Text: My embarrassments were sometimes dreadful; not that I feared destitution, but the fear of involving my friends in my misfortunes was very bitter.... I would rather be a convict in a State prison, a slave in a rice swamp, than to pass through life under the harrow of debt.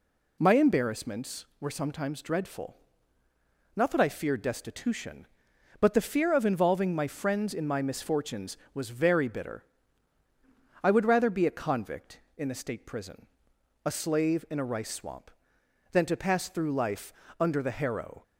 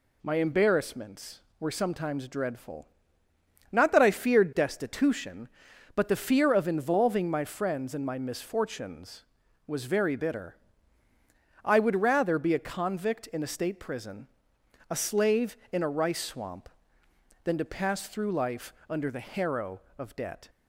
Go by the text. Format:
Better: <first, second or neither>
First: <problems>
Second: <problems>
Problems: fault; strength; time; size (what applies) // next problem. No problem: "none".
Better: second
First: pauses between "life" and "under"; slight; at 17.1 s; 0.26 s long // stops before "of debt"; at 18.2 s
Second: pauses between "life" and "under"; slight; at 18.7 s; 0.18 s long